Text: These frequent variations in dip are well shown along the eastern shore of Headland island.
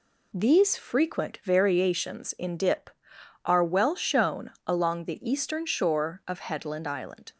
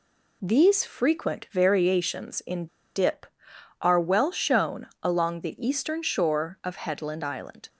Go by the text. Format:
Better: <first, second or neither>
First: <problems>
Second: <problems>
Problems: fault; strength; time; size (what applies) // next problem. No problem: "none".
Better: first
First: pauses between "shown" and "along"; slight; at 4.5 s; 0.16 s long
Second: pauses between "in" and "dip"; slight; at 2.6 s; 0.29 s long // pauses between "shown" and "along"; slight; at 4.8 s; 0.16 s long